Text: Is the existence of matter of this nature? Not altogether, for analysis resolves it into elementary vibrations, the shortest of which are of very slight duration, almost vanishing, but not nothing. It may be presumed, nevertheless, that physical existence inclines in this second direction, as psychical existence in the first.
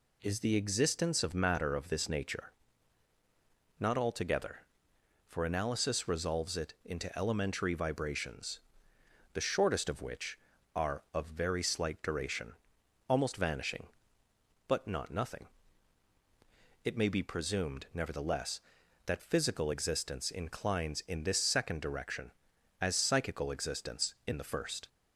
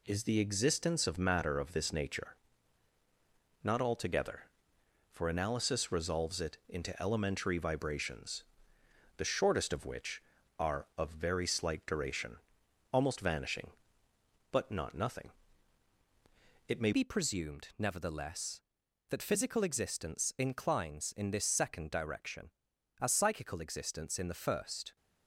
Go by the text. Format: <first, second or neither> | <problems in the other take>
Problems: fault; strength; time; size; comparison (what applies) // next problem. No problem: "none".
first | changes voice at "be"; from 16.9 s on; 8.0 s long